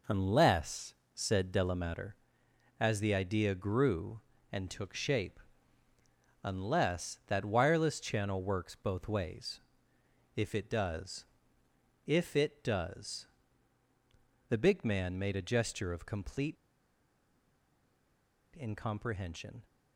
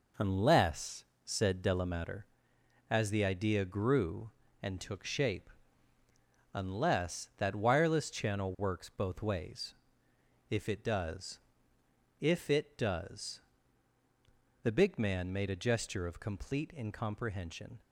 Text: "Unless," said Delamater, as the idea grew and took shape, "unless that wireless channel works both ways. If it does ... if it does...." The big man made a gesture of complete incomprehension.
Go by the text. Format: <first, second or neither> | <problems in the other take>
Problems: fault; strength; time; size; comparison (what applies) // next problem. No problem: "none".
second | pauses between "complete" and "incomprehension"; strong; at 16.5 s; 2.0 s long